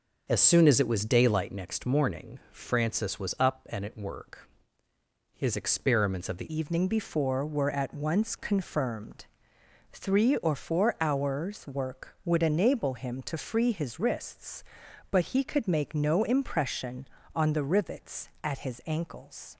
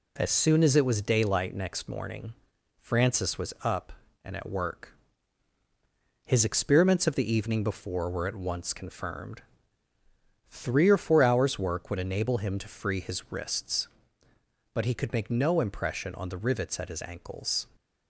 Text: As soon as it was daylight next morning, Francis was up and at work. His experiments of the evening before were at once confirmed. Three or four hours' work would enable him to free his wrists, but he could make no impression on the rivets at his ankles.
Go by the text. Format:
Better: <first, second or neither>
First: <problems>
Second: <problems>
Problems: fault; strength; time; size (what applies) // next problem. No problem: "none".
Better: second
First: starts louder than the rest; until 1.2 s; 6.5 dB // changes voice at "evening"; from 6.5 s on; 13.0 s long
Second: none